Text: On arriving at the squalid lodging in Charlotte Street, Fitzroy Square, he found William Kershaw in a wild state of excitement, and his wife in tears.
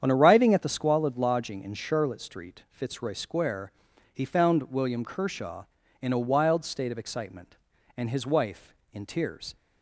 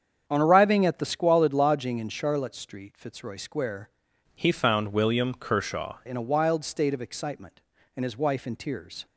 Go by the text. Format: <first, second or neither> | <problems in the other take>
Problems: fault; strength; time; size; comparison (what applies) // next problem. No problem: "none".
first | starts louder than the rest; strong; until 1.2 s; 7.5 dB; strong in the first // changes voice from "he" to "Kershaw"; from 4.3 to 5.9 s; 1.6 s long